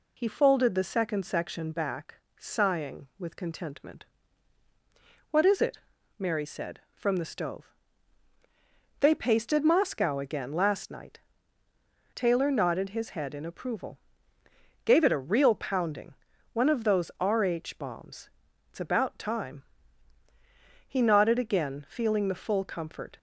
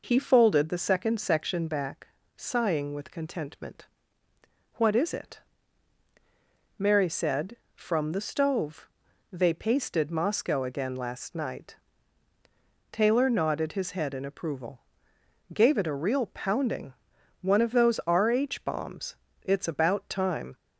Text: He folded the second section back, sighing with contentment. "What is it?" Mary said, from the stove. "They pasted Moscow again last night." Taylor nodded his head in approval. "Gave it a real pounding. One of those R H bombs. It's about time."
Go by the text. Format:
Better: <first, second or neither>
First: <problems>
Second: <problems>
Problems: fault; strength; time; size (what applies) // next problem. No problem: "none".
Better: second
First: goes on to say "He nodded again feeling the full comfort"; strong; from 20.8 s on; 2.3 s long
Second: none